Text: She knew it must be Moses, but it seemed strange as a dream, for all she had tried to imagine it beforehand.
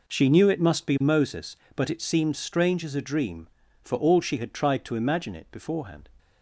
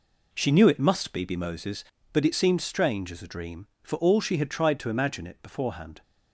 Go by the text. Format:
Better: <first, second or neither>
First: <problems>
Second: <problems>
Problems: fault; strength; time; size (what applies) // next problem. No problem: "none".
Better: first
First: none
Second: says "be" twice; at 1.2 s